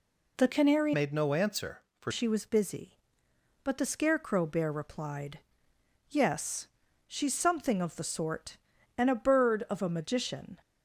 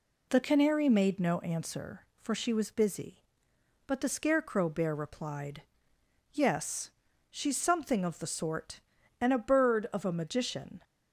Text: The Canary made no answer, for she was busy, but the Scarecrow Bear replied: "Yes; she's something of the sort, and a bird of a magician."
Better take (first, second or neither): second